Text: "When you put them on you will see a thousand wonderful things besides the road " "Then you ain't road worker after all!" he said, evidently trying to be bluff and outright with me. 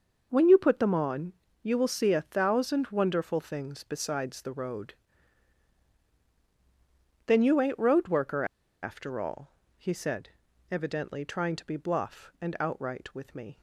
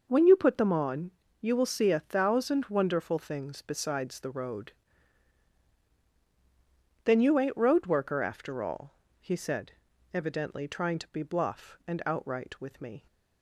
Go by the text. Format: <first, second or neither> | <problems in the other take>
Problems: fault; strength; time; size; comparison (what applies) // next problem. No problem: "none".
second | starts louder than the rest; until 1.3 s; 6.5 dB; also in the second // pauses between "on" and "you"; slight; at 1.3 s; 0.28 s long; slight in the second // pauses between "worker" and "after"; at 8.4 s; 0.38 s long